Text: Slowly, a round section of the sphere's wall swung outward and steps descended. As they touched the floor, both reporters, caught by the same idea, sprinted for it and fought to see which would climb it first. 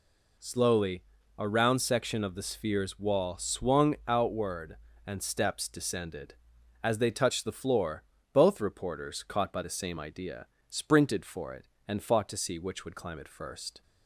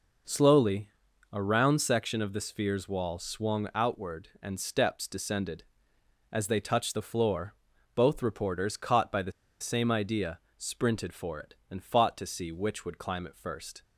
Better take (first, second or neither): first